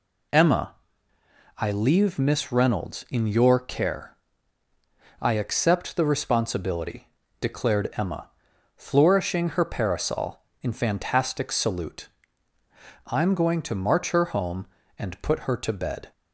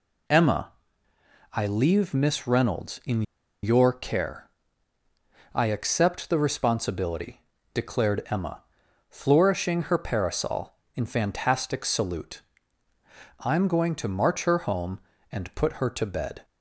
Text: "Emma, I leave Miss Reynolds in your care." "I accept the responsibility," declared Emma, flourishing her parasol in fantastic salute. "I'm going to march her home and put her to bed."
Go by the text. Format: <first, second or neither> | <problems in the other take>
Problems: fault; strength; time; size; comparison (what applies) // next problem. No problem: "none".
first | pauses between "in" and "your"; at 3.2 s; 0.40 s long